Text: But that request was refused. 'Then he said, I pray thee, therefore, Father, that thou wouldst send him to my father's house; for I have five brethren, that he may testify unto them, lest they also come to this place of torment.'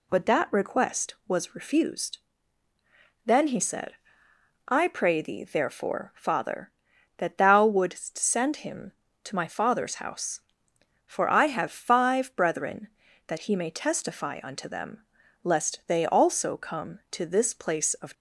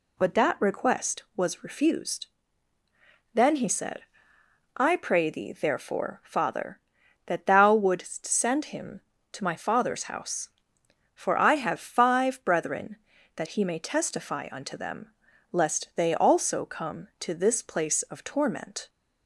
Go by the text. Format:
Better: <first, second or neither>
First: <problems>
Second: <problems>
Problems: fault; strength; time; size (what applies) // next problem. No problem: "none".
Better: second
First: stops before "torment"; at 18.1 s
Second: none